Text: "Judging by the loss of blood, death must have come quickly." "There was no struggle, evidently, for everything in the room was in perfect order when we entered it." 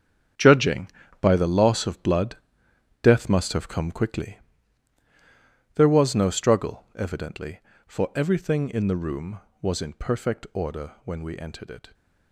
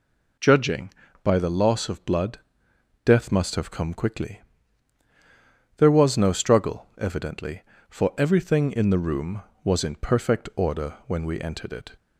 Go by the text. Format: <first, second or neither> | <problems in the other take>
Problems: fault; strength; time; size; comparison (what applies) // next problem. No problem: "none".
second | gets quieter; strong; throughout; 12.5 dB